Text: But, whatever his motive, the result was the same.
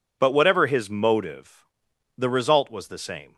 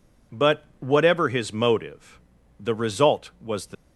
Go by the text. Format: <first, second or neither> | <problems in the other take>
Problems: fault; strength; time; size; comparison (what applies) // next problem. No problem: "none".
first | stops before "same"; at 3.7 s